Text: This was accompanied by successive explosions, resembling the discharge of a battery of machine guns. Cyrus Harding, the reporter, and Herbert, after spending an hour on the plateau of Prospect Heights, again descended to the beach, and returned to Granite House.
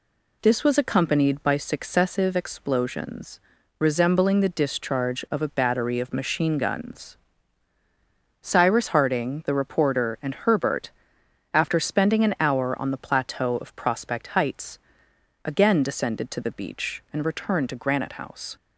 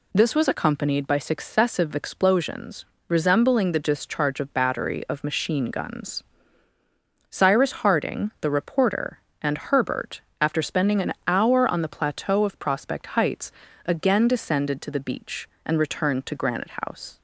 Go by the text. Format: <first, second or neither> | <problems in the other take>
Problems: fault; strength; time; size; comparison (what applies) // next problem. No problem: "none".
first | skips "a"; at 4.5 s // pauses between "an" and "hour"; slight; at 11.1 s; 0.16 s long